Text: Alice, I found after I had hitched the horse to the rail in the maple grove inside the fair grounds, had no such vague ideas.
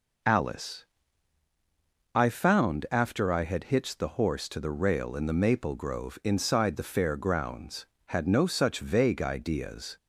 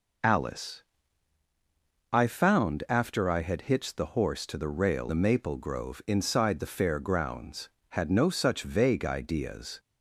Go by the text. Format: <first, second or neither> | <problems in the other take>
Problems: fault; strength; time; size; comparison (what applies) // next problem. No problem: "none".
first | skips "in"; at 5.0 s